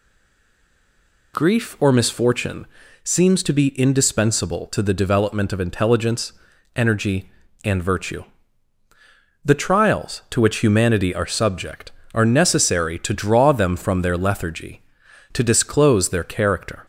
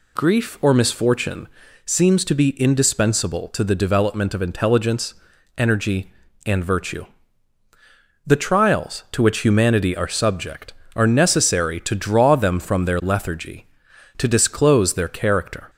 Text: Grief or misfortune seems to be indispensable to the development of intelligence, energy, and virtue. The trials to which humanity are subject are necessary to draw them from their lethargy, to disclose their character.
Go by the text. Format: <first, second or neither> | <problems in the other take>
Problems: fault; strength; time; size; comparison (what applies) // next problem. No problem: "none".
second | stays silent before the first word; noticeable; until 1.3 s; 1.3 s long // pauses between "misfortune" and "seems"; at 2.6 s; 0.38 s long; also in the second